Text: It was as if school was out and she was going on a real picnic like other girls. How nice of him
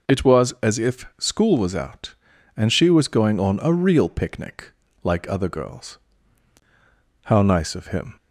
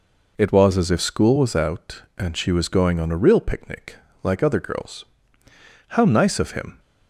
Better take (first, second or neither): neither